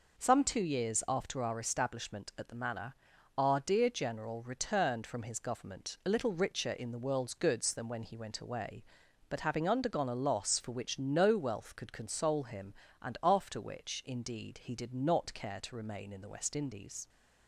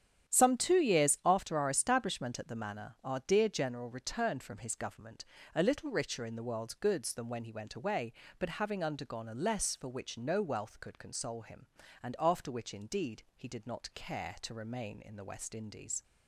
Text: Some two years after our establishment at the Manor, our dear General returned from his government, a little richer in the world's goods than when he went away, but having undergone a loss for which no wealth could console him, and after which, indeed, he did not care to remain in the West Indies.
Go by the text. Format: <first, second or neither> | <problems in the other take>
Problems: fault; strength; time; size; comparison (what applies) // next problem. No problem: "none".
first | starts louder than the rest; strong; until 1.3 s; 9.5 dB // says "less" for "loss"; at 9.3 s